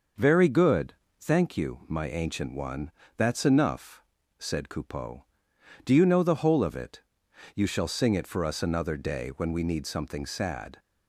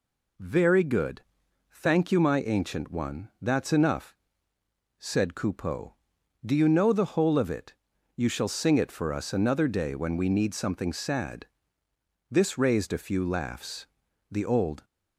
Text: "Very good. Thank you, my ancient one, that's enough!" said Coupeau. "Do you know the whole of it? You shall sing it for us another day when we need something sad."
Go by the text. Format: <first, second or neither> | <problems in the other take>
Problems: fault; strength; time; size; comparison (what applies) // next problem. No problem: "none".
first | goes on to say "This raised a few laughs The old"; strong; from 12.2 s on; 2.5 s long